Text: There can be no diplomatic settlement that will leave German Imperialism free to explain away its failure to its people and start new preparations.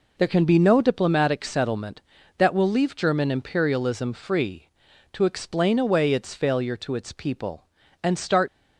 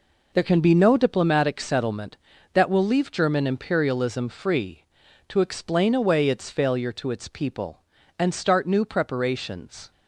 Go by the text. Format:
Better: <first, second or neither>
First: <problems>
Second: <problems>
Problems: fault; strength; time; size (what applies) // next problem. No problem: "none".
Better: second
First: stops before "new preparations"; at 8.4 s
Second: none